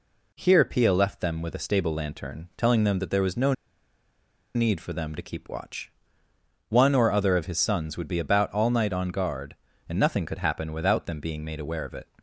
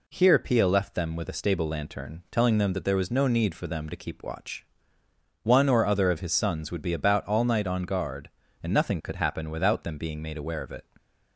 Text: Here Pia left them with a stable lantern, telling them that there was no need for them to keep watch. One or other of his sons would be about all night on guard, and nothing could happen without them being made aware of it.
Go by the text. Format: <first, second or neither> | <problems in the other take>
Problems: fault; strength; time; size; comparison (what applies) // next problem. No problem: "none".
second | pauses between "no" and "need"; at 3.5 s; 1.0 s long